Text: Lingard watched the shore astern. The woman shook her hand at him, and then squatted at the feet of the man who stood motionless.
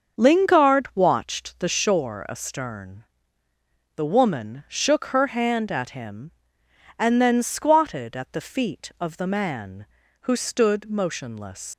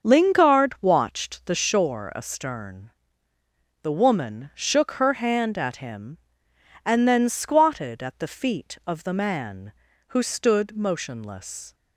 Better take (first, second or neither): second